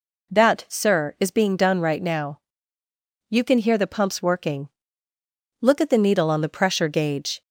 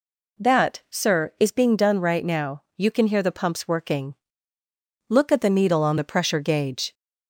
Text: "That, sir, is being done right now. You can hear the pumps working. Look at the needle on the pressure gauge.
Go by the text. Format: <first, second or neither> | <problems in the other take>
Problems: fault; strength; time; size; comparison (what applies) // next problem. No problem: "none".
neither | none